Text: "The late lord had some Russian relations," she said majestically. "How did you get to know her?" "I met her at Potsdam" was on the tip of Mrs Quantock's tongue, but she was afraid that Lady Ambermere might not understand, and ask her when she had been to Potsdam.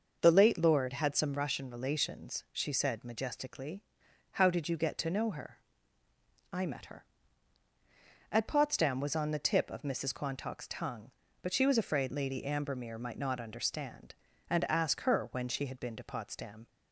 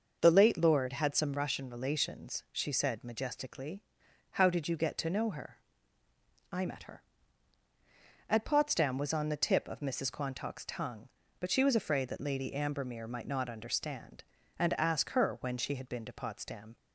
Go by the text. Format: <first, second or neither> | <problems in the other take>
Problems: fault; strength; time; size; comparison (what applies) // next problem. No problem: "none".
second | starts louder than the rest; until 1.2 s; 6.5 dB; also in the second // skips "that"; at 12.1 s